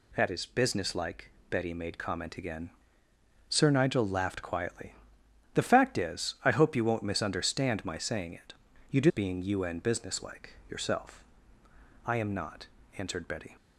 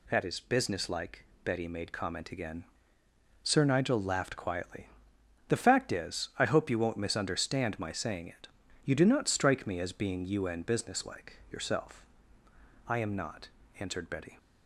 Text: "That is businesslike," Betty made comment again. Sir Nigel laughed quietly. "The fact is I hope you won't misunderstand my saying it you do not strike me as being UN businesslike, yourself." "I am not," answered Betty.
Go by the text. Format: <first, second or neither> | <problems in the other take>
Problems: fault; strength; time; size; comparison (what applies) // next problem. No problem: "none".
second | pauses between "it" and "you"; at 8.5 s; 0.38 s long; also in the second // skips "not strike me as"; at 9.0 s